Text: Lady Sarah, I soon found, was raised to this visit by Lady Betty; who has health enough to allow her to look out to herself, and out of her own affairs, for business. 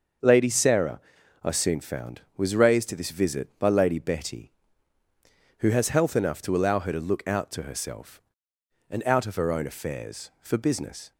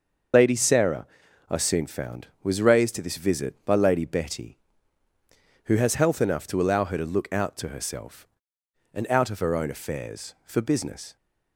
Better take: first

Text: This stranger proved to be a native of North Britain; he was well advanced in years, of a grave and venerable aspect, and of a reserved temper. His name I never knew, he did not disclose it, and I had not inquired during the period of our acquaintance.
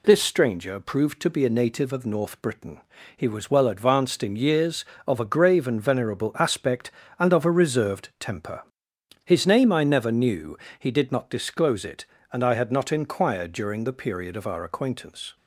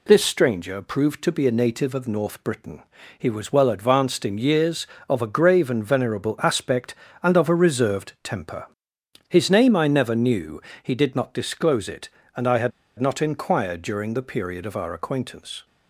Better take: first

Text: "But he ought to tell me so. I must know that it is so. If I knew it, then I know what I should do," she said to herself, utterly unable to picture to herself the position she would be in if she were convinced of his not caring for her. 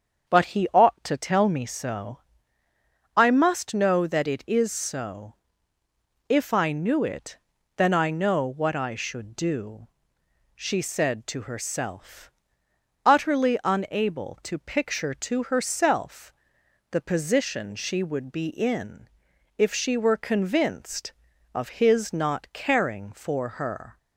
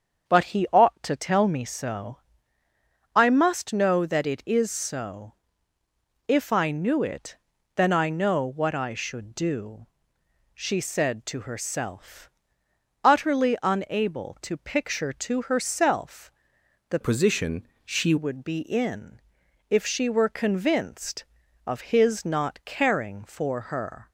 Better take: first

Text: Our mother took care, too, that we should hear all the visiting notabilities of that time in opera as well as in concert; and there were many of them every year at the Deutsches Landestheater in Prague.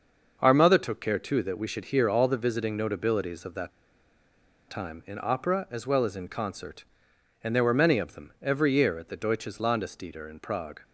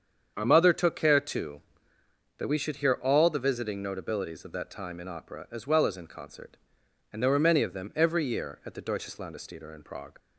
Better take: second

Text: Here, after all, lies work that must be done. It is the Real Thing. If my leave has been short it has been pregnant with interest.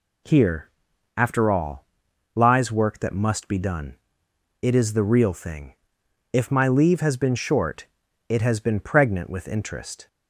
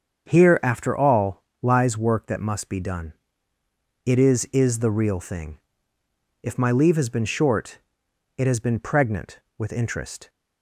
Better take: first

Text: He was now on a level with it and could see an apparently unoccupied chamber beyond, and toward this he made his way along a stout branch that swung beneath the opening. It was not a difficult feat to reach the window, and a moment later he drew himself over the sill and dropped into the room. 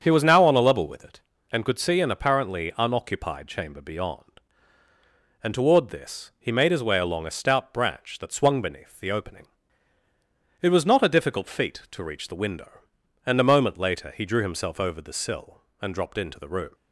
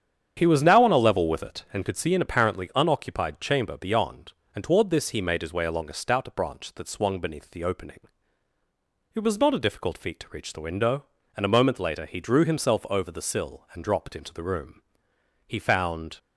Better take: first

